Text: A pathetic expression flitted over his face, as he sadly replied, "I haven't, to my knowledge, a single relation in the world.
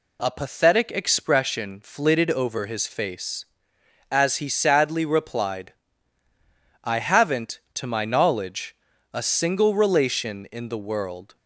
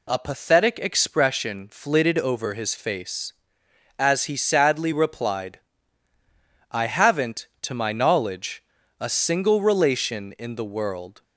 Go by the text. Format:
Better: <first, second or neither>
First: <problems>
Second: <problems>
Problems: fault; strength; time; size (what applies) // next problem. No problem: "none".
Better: neither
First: none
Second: none